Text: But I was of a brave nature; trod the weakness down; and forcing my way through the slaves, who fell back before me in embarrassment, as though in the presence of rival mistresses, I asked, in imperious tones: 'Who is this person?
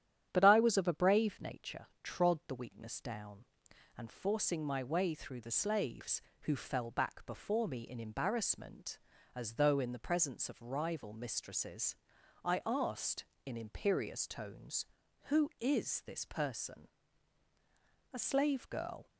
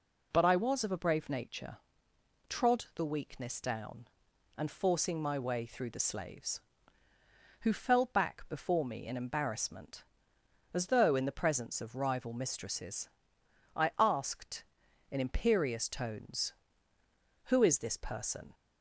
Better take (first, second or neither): second